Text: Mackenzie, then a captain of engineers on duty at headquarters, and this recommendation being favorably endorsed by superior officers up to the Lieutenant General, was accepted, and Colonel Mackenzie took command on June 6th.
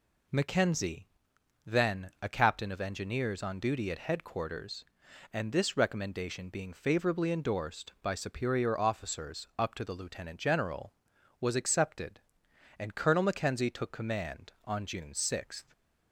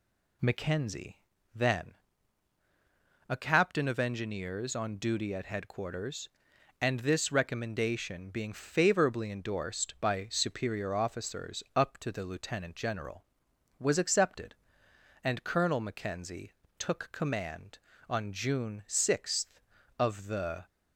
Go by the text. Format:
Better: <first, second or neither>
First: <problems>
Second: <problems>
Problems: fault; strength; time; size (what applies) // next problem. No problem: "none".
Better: first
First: none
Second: pauses between "then" and "a"; strong; at 1.9 s; 1.3 s long // pauses between "Mackenzie" and "took"; slight; at 16.5 s; 0.26 s long // goes on to say "Of the"; noticeable; from 19.9 s on; 0.66 s long